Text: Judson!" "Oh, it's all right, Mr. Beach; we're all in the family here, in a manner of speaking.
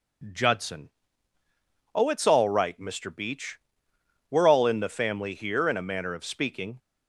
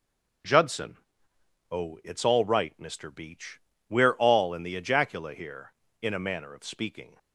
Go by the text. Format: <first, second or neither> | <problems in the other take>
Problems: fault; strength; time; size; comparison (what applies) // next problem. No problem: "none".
first | says "ejacula" for "family"; at 4.7 s